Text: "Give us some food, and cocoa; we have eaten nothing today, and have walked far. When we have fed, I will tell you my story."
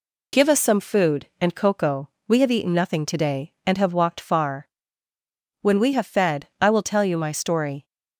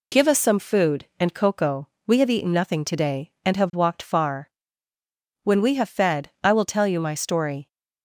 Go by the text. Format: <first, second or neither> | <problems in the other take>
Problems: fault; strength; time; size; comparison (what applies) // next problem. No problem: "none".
neither | none